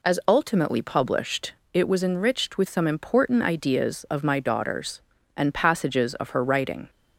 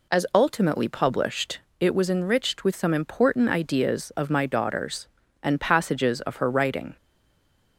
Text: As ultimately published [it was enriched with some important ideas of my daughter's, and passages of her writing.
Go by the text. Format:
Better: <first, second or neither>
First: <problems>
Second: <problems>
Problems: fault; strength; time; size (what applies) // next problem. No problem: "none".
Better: first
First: pauses between "published" and "it"; slight; at 1.5 s; 0.18 s long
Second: pauses between "published" and "it"; slight; at 1.6 s; 0.18 s long // stays silent after the last word; slight; from 6.9 s on; 0.8 s long